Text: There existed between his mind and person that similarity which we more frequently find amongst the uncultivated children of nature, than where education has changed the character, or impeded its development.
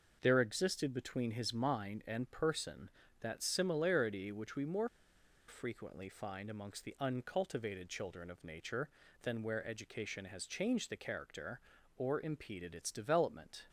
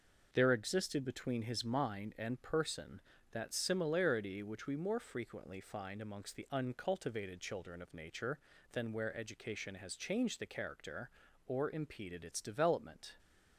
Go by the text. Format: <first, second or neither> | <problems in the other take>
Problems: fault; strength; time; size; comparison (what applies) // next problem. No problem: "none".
second | pauses between "more" and "frequently"; noticeable; at 4.8 s; 0.60 s long